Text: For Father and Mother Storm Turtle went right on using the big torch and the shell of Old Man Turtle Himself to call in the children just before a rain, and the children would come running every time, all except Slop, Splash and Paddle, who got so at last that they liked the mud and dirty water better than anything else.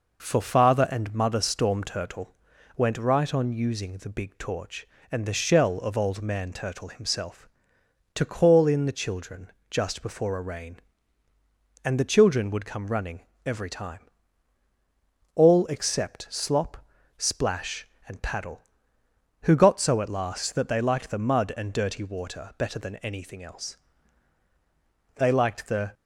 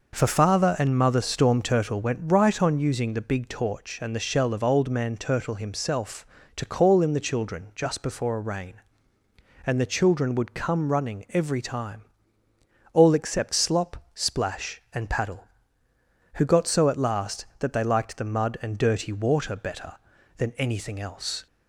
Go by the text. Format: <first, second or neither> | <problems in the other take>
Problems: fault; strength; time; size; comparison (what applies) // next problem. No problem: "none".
second | pauses between "Turtle" and "went"; at 2.3 s; 0.42 s long // pauses between "children" and "just"; slight; at 9.4 s; 0.22 s long // pauses between "running" and "every"; slight; at 13.2 s; 0.24 s long // goes on to say "They liked the"; noticeable; from 25.1 s on; 0.78 s long